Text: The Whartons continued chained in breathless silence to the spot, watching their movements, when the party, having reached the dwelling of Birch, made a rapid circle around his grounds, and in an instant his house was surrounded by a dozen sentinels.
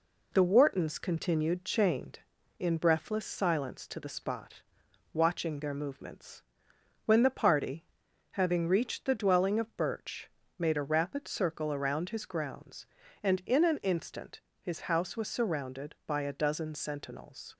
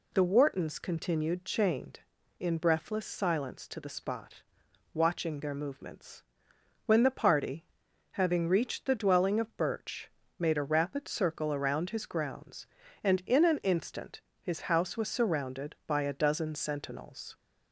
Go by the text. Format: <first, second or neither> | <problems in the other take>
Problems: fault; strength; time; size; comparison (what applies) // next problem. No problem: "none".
second | gets quieter; slight; throughout; 3 dB // pauses between "instant" and "his"; slight; at 14.3 s; 0.22 s long; slight in the second